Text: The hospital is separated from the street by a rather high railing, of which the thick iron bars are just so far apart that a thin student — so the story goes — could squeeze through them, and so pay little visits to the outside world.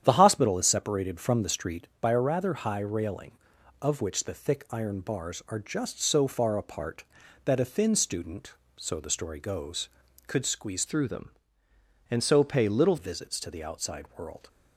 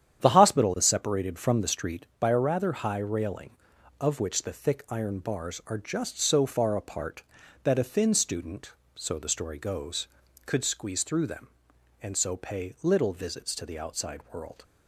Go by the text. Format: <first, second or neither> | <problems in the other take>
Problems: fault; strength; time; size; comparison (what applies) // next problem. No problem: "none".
second | starts louder than the rest; strong; until 1.0 s; 9.5 dB; strong in the second // changes voice from "through" to "little"; from 10.8 to 12.9 s; 2.1 s long